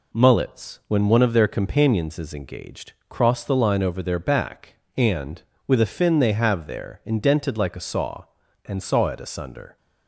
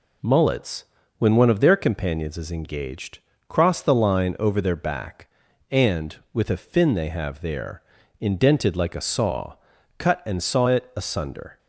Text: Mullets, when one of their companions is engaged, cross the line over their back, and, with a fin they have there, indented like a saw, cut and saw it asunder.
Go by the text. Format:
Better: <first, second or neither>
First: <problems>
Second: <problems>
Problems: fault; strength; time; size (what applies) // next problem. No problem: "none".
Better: second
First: skips "cut"; at 8.4 s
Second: none